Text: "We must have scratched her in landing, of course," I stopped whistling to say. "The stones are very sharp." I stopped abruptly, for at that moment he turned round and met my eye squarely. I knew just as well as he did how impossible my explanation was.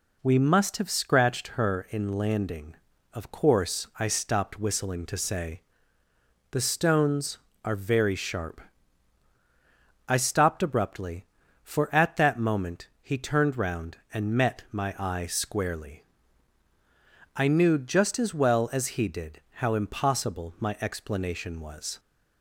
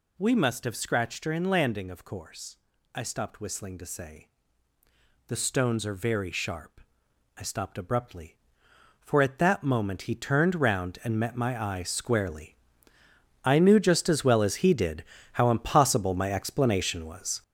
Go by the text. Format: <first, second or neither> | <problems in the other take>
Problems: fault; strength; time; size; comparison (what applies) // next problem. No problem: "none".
first | gets louder; strong; throughout; 7.5 dB // pauses between "did" and "how"; slight; at 15.0 s; 0.28 s long